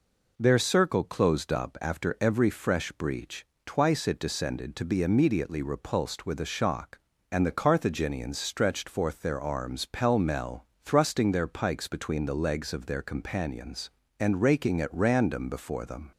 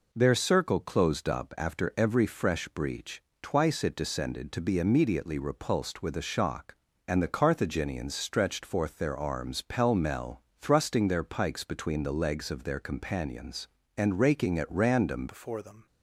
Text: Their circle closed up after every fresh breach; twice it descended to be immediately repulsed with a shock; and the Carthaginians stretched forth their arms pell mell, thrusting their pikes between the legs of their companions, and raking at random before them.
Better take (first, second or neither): first